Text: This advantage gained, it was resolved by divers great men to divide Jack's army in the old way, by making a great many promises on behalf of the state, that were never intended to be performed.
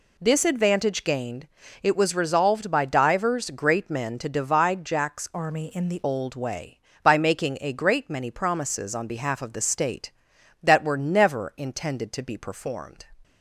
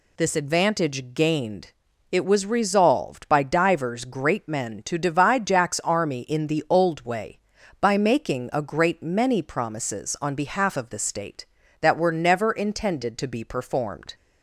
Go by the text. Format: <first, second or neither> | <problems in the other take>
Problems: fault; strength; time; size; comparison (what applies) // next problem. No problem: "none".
second | changes voice from "army" to "the"; from 5.3 to 6.0 s; 0.7 s long